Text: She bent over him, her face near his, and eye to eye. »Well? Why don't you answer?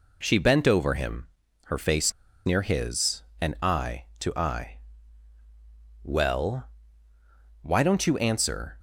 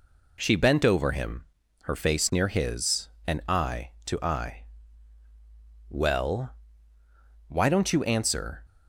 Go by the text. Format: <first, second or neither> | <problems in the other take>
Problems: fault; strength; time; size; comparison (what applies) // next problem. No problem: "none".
second | pauses between "face" and "near"; slight; at 2.1 s; 0.34 s long